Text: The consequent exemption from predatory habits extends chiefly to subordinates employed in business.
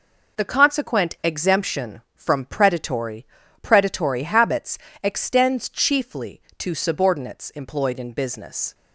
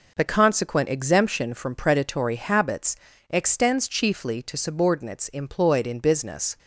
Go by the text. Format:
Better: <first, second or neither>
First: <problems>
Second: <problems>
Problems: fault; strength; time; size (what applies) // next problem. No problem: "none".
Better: second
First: says "predatory" twice; at 3.6 s // pauses between "habits" and "extends"; slight; at 4.7 s; 0.24 s long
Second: pauses between "habits" and "extends"; slight; at 2.9 s; 0.34 s long